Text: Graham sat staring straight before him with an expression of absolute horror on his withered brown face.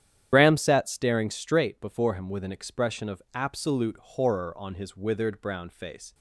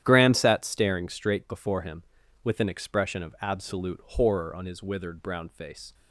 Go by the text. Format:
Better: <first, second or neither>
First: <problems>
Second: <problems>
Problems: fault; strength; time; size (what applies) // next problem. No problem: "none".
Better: second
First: loses the start of "Graham"; at 0.3 s; 65 ms // starts louder than the rest; strong; until 1.3 s; 10.5 dB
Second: starts louder than the rest; strong; until 1.0 s; 11 dB